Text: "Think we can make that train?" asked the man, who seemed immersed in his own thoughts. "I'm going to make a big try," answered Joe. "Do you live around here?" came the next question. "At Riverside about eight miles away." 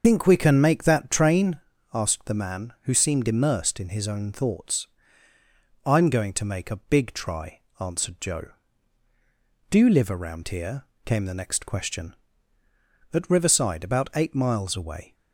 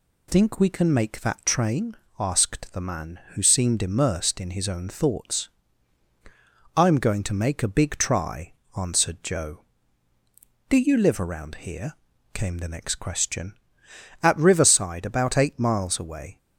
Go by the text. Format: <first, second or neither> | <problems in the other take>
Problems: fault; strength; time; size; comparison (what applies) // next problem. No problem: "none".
second | loses the start of "Think"; at 0.0 s; 105 ms // starts louder than the rest; until 1.0 s; 6.5 dB